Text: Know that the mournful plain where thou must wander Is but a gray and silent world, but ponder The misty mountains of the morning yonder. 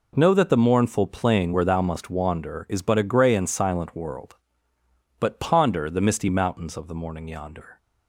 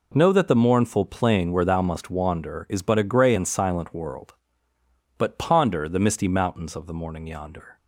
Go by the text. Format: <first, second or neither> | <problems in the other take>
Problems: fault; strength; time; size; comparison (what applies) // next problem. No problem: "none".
neither | none